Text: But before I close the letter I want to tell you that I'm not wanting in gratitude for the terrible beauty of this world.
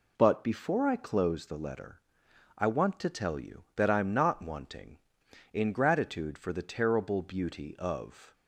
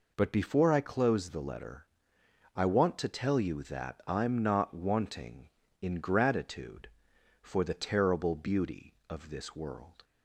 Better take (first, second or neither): second